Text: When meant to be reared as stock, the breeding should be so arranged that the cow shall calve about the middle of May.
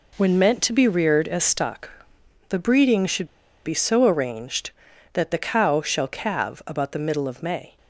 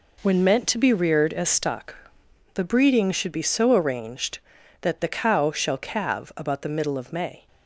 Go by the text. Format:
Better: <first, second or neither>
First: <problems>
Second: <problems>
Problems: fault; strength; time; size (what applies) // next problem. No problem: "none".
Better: second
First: pauses between "should" and "be"; at 3.2 s; 0.39 s long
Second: none